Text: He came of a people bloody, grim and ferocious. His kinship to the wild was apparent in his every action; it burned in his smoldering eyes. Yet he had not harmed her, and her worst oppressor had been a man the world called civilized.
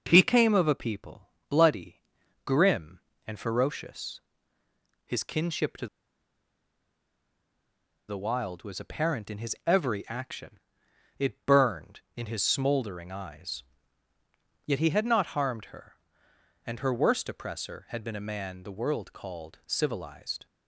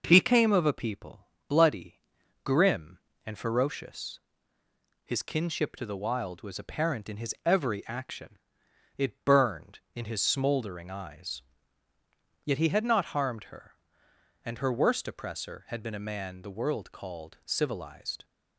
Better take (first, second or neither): second